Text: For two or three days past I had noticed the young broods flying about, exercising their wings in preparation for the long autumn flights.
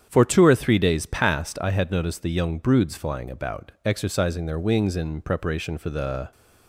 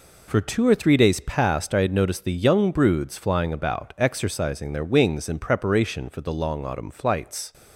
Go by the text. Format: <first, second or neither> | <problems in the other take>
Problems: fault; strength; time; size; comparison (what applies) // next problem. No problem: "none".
second | starts louder than the rest; strong; until 1.1 s; 8.5 dB // stops before "long autumn flights"; at 6.3 s